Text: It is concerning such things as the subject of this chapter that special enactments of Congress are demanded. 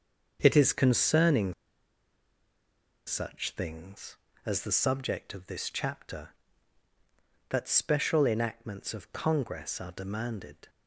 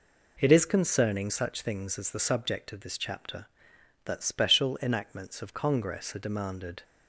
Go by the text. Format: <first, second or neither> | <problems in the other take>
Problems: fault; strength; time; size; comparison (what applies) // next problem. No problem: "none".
second | starts louder than the rest; until 1.4 s; 6.5 dB // pauses between "concerning" and "such"; strong; at 1.5 s; 1.5 s long